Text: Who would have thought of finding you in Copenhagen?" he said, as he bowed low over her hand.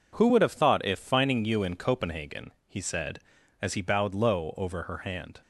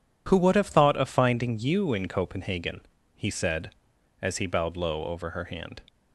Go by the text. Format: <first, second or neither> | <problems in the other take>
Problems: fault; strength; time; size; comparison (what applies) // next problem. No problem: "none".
second | says "if" for "of"; at 0.8 s